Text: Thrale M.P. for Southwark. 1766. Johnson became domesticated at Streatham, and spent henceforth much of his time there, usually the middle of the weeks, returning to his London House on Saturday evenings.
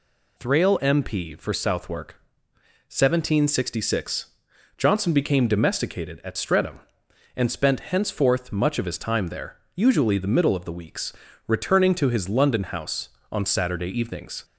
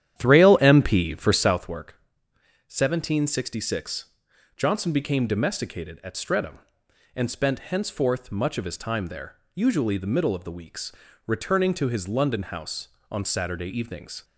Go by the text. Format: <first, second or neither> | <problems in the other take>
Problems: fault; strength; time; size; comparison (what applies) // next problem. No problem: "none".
first | starts louder than the rest; strong; until 1.7 s; 10.5 dB